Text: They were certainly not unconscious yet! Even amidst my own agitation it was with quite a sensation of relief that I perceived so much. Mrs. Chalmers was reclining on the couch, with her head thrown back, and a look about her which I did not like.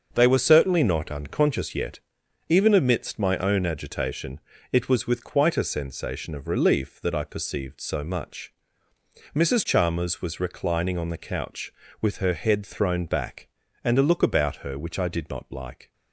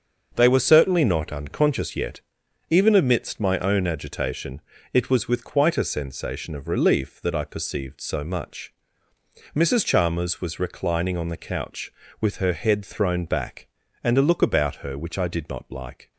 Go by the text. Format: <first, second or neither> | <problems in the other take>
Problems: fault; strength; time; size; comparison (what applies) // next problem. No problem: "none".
neither | starts louder than the rest; the same in both // pauses between "agitation" and "it"; slight; the same in both